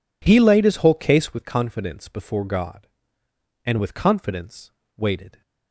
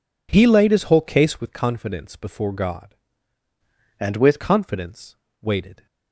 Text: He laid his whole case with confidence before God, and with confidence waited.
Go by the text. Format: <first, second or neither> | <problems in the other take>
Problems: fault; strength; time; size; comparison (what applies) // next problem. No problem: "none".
first | changes voice from "and" to "with"; from 4.0 to 4.4 s; 0.4 s long // pauses between "confidence" and "waited"; slight; at 5.1 s; 0.26 s long; slight in the first